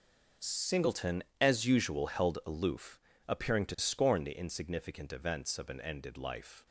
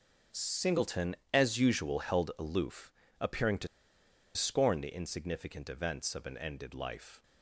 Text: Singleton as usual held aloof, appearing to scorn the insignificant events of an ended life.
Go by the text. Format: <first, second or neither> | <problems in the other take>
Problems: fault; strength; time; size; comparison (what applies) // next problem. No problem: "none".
first | pauses between "to" and "scorn"; noticeable; at 3.6 s; 0.69 s long